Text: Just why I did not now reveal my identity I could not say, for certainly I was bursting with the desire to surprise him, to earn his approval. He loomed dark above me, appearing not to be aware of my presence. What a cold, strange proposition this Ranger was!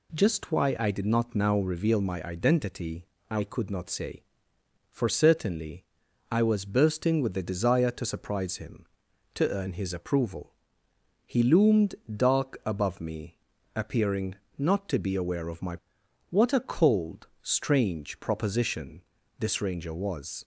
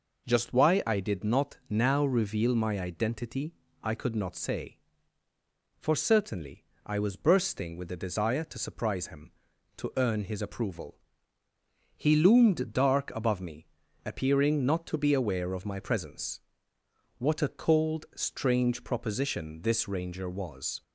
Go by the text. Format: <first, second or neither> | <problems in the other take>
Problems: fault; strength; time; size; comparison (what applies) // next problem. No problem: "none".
second | pauses between "identity" and "I"; slight; at 3.0 s; 0.24 s long; slight in the second // pauses between "certainly" and "I"; at 5.8 s; 0.44 s long; slight in the second // pauses between "loomed" and "dark"; slight; at 11.9 s; 0.18 s long // pauses between "appearing" and "not"; slight; at 14.3 s; 0.24 s long // skips "presence"; at 16.0 s // pauses between "proposition" and "this"; at 19.0 s; 0.38 s long